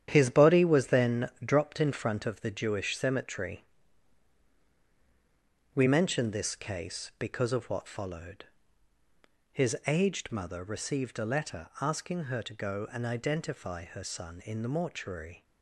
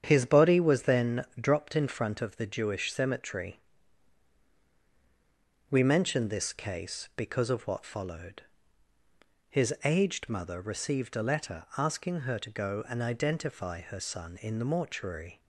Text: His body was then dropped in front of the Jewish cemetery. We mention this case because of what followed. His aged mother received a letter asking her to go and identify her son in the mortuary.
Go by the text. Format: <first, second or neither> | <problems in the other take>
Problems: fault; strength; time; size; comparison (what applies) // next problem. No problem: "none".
second | gets quieter; strong; throughout; 8.5 dB // starts louder than the rest; strong; until 1.1 s; 9.5 dB; strong in the second // pauses between "then" and "dropped"; slight; at 1.2 s; 0.16 s long; slight in the second